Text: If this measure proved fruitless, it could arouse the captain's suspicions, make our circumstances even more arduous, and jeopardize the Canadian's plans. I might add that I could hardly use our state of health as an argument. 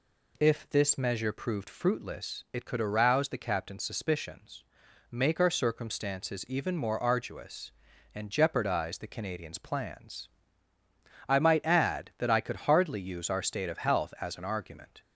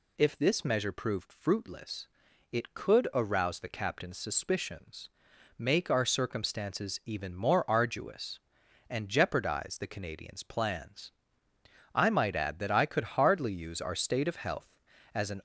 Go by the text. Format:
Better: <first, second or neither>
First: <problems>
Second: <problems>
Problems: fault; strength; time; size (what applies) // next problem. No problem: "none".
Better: first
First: none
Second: stops before "argument"; at 15.3 s